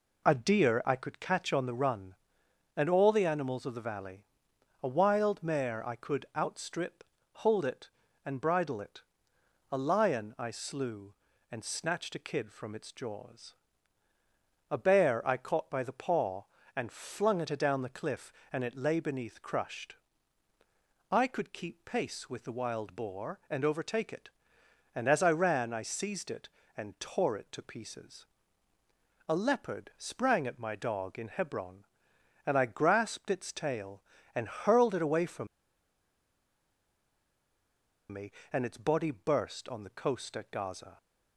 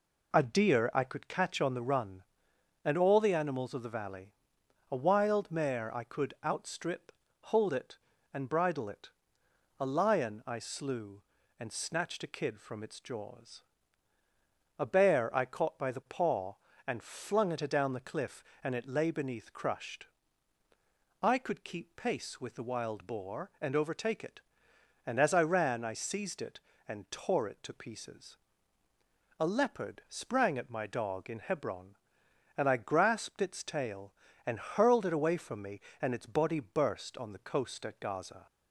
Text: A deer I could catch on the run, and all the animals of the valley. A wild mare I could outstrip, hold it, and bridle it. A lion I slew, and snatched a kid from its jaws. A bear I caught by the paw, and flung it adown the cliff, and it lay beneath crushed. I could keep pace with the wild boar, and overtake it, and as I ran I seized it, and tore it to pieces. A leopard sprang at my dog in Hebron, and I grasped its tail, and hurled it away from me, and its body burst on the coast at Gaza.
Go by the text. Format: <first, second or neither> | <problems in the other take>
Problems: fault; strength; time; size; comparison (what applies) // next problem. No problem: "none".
second | pauses between "from" and "me"; strong; at 35.4 s; 2.6 s long